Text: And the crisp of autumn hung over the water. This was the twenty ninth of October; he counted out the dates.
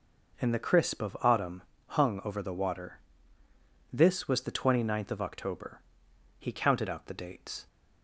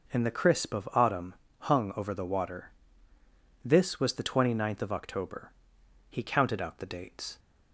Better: neither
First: pauses between "autumn" and "hung"; slight; at 1.6 s; 0.26 s long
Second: pauses between "autumn" and "hung"; slight; at 1.3 s; 0.26 s long

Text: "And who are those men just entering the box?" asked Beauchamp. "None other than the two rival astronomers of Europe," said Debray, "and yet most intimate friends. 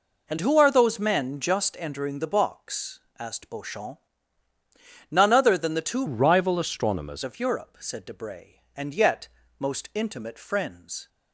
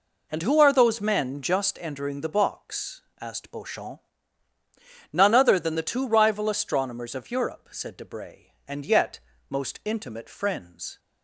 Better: second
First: changes voice from "rival" to "astronomers"; from 6.0 to 7.2 s; 1.2 s long // pauses between "yet" and "most"; slight; at 9.2 s; 0.30 s long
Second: pauses between "yet" and "most"; slight; at 9.1 s; 0.29 s long

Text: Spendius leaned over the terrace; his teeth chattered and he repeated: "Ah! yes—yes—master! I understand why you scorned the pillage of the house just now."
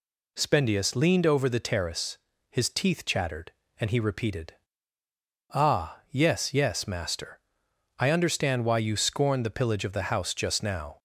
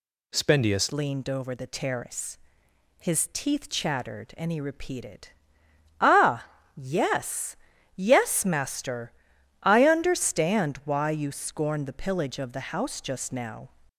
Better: first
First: none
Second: changes voice at "leaned"; from 0.9 s on; 12.7 s long

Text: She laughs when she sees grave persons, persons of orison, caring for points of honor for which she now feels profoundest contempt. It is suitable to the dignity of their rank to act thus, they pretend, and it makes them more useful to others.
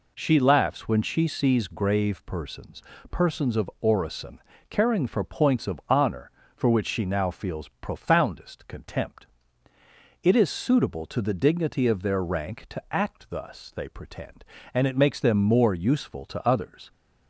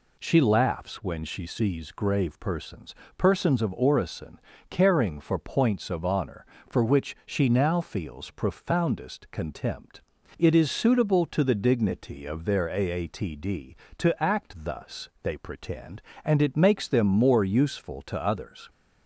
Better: first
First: none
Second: says "aatd" for "rank"; at 12.6 s

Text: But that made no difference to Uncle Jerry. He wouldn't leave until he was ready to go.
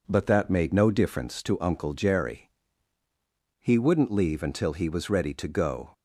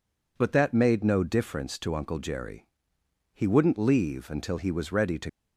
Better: first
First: none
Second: stops before "go"; at 5.2 s

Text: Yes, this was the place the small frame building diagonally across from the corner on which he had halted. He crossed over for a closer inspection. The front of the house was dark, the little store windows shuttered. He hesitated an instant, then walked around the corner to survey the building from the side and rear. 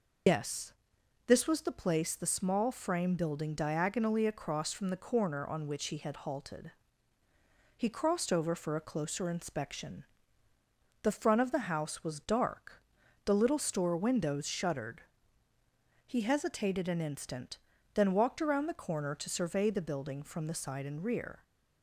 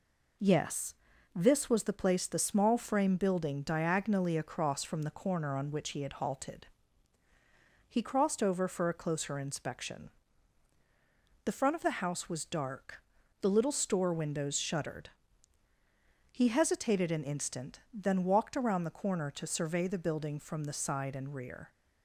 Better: second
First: loses the start of "Yes"; at 0.2 s; 120 ms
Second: none

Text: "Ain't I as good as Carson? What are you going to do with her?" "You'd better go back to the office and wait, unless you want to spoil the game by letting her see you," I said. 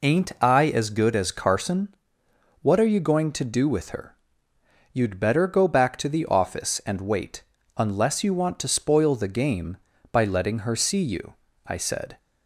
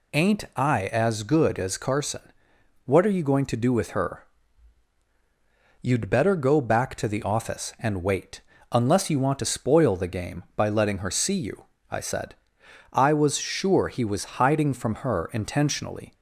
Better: first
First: none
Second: goes on to say "I was sure he was hiding from her intentionally"; strong; from 12.9 s on; 3.2 s long

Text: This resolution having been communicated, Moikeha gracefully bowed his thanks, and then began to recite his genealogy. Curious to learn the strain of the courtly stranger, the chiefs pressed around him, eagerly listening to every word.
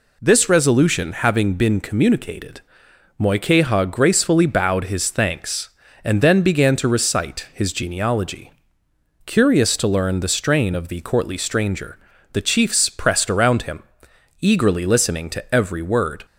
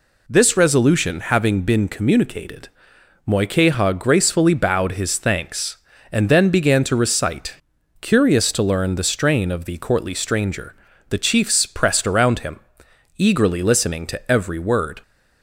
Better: first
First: none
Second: skips "his genealogy"; at 7.7 s

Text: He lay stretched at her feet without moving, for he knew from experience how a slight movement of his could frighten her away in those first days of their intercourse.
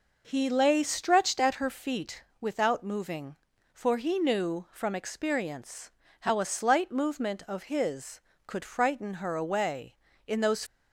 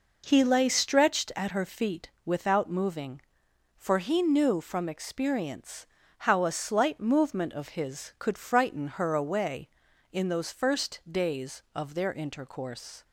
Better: second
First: pauses between "feet" and "without"; slight; at 2.2 s; 0.16 s long // pauses between "experience" and "how"; slight; at 5.9 s; 0.30 s long // stops before "first days of their intercourse"; at 10.6 s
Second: pauses between "feet" and "without"; slight; at 2.0 s; 0.16 s long // pauses between "experience" and "how"; slight; at 5.8 s; 0.34 s long

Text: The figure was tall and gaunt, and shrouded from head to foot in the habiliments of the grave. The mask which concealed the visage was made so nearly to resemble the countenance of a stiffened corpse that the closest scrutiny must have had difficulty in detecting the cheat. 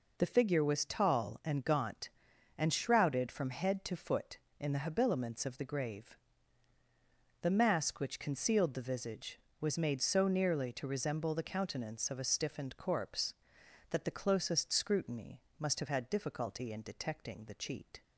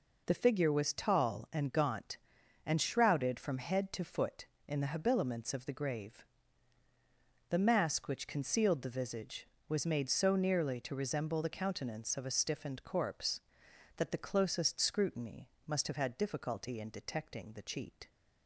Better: neither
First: pauses between "scrutiny" and "must"; slight; at 15.4 s; 0.18 s long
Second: pauses between "scrutiny" and "must"; slight; at 15.4 s; 0.18 s long

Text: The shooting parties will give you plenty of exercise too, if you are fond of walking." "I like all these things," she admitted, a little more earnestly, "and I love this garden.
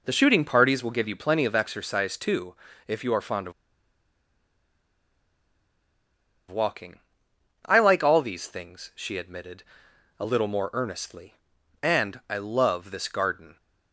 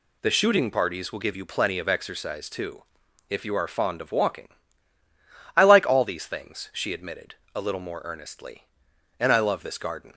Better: second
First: pauses between "of" and "walking"; strong; at 3.5 s; 2.9 s long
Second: none

